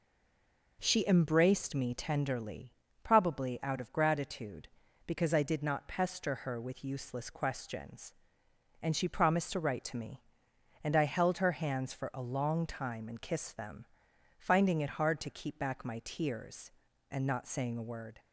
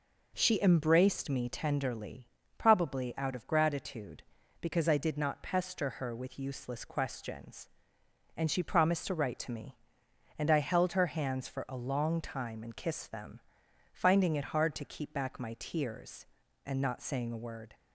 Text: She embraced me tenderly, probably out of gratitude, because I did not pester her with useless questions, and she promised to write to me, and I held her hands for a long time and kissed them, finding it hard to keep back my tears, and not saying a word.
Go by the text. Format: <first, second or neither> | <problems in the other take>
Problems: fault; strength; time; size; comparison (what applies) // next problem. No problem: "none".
second | stays silent before the first word; slight; until 0.7 s; 0.7 s long